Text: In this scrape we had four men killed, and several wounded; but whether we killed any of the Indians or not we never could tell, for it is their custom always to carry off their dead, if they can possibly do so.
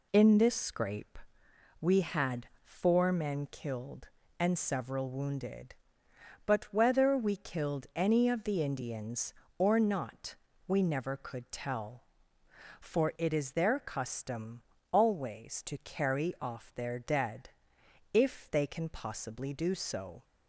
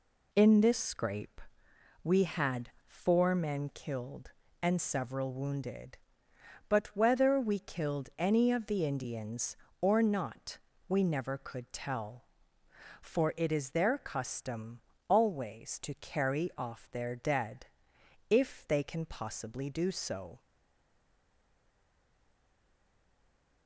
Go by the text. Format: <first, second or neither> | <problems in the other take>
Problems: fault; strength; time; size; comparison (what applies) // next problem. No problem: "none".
first | pauses between "scrape" and "we"; noticeable; at 1.4 s; 0.62 s long; noticeable in the first // pauses between "had" and "four"; slight; at 2.6 s; 0.18 s long; slight in the first // pauses between "not" and "we"; slight; at 10.5 s; 0.30 s long; slight in the first // pauses between "custom" and "always"; slight; at 14.8 s; 0.26 s long; slight in the first // stays silent after the last word; strong; from 20.3 s on; 3.3 s long